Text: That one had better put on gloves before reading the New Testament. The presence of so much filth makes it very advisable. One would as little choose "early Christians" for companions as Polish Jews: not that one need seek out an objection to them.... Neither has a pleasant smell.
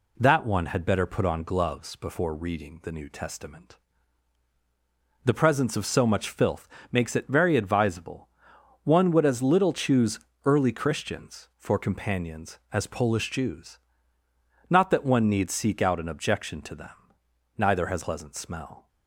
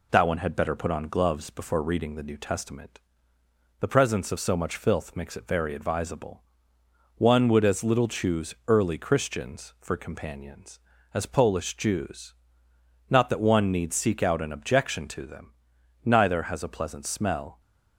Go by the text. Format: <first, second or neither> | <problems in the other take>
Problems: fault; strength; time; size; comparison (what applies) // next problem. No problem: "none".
second | pauses between "filth" and "makes"; slight; at 6.6 s; 0.24 s long // pauses between "choose" and "early"; slight; at 10.2 s; 0.24 s long // skips "a"; at 18.0 s